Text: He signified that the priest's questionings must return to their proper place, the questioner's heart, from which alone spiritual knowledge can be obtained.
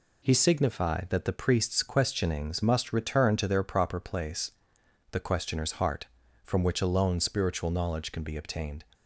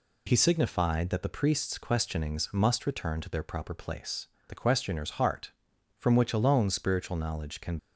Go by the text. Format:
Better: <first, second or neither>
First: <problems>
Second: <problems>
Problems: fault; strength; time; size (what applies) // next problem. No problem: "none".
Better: first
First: none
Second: stops before "be obtained"; at 7.7 s